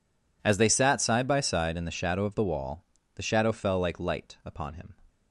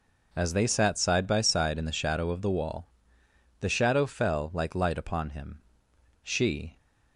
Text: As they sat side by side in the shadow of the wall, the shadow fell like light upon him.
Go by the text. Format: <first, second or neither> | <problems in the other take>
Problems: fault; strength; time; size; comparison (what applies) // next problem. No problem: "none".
first | goes on to say "She"; from 6.2 s on; 0.54 s long